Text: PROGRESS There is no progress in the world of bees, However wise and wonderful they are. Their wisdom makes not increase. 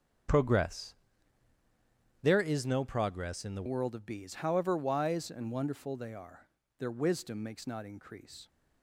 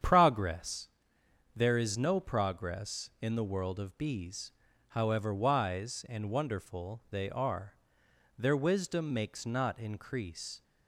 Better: second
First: starts louder than the rest; strong; until 2.5 s; 7.5 dB // pauses between "PROGRESS" and "There"; strong; at 0.9 s; 1.2 s long // changes voice at "world"; from 3.6 s on; 4.8 s long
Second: starts louder than the rest; strong; until 1.6 s; 8.5 dB // pauses between "PROGRESS" and "There"; noticeable; at 0.8 s; 0.66 s long

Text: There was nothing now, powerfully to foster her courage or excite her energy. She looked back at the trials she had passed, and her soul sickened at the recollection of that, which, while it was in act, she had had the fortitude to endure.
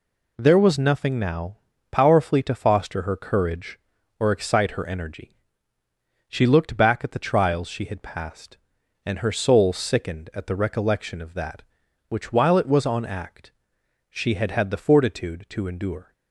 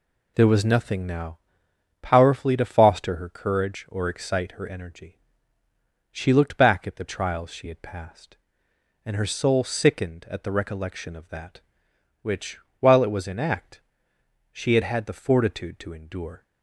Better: second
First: says "on" for "in"; at 12.8 s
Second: none

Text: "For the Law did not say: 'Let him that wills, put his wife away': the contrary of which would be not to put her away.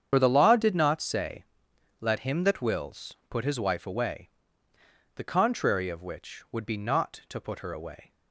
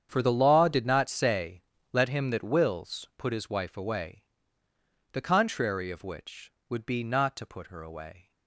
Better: second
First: loses the start of "For"; at 0.1 s; 65 ms // starts louder than the rest; strong; until 1.1 s; 8 dB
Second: starts louder than the rest; strong; until 1.1 s; 8 dB

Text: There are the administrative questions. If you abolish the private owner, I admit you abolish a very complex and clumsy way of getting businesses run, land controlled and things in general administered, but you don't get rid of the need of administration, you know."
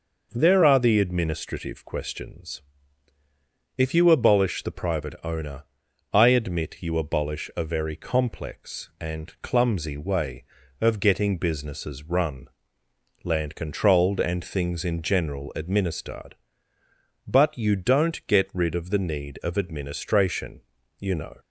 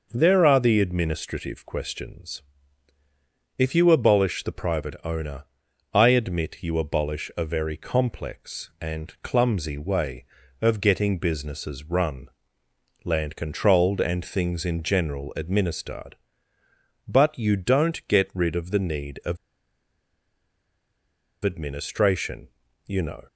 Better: first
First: none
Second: pauses between "of" and "administration"; strong; at 19.3 s; 2.0 s long

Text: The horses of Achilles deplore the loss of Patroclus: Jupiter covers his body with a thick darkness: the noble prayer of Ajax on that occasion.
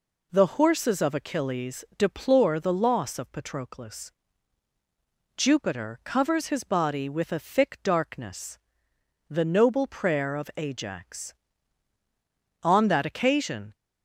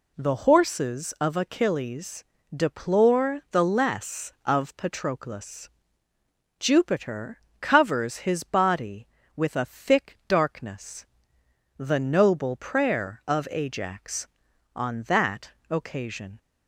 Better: first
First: none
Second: pauses between "Achilles" and "deplore"; slight; at 2.2 s; 0.34 s long // says "less" for "loss"; at 3.6 s // pauses between "Jupiter" and "covers"; slight; at 7.3 s; 0.20 s long // pauses between "that" and "occasion"; slight; at 15.4 s; 0.18 s long

